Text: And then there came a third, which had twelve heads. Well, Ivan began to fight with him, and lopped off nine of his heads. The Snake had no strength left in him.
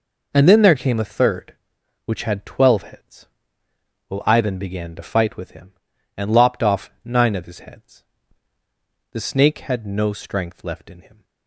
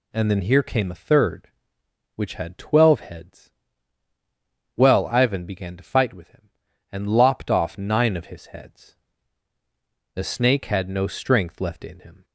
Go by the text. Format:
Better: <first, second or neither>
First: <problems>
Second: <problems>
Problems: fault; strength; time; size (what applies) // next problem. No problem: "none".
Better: first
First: none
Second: says "here" for "there"; at 0.4 s